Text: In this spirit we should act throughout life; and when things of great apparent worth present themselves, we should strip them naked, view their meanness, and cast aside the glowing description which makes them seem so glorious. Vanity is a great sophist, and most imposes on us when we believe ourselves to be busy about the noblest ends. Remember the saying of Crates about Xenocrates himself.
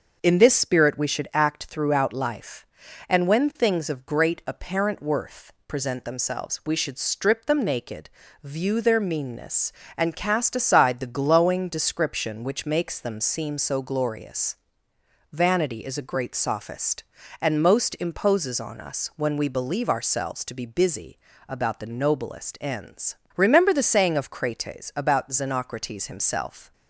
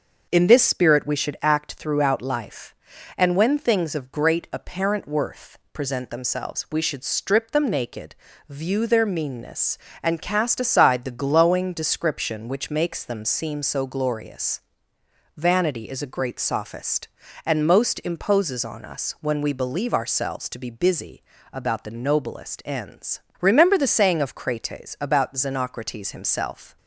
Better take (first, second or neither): neither